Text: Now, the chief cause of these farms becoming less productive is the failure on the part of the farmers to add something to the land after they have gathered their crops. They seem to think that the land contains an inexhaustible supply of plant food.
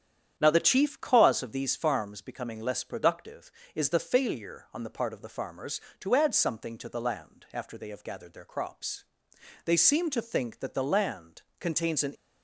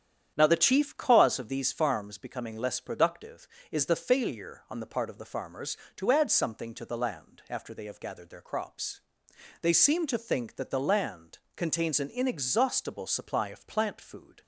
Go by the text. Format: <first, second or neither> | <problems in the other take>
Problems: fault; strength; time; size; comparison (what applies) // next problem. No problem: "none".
second | starts louder than the rest; strong; until 1.3 s; 9 dB; strong in the second // pauses between "land" and "contains"; slight; at 11.4 s; 0.18 s long; slight in the second // stops before "inexhaustible supply of plant food"; at 12.1 s